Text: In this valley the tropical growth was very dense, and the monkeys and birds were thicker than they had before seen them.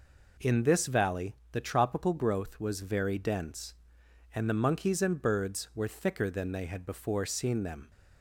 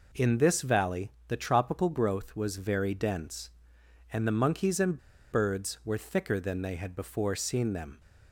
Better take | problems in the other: first | pauses between "valley" and "the"; slight; at 1.0 s; 0.18 s long; slight in the first // pauses between "and" and "birds"; slight; at 4.9 s; 0.32 s long

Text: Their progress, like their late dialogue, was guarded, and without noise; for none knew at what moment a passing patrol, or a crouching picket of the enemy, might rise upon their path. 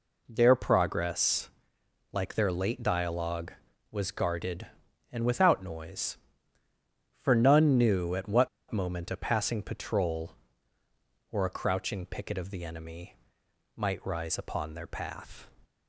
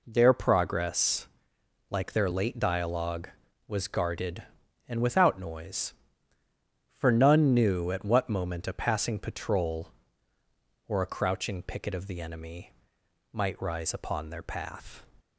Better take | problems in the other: second | pauses between "what" and "moment"; slight; at 8.4 s; 0.22 s long

